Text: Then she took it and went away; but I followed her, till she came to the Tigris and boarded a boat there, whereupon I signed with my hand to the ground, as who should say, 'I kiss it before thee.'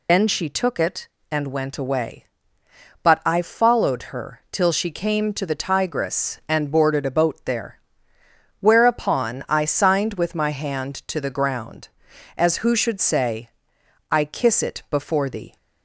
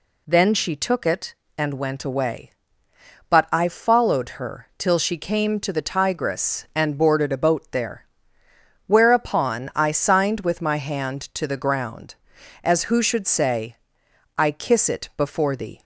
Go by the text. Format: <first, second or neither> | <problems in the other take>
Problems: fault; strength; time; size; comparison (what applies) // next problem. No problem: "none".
second | loses the start of "Then"; at 0.0 s; 95 ms